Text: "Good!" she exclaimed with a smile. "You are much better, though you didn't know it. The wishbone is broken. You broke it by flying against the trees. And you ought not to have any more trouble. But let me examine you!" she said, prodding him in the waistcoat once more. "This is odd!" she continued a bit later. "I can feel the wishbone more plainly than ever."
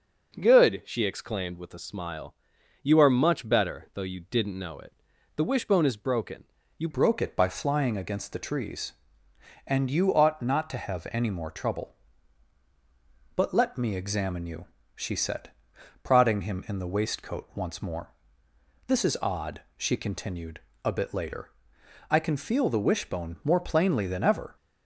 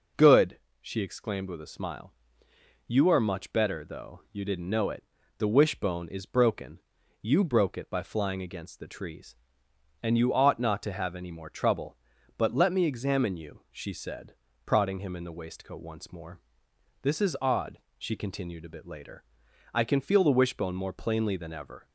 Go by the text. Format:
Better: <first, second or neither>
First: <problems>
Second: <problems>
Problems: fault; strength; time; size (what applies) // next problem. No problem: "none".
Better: second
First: changes voice at "broke"; from 6.9 s on; 17.6 s long // pauses between "continued" and "a"; slight; at 20.5 s; 0.24 s long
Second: none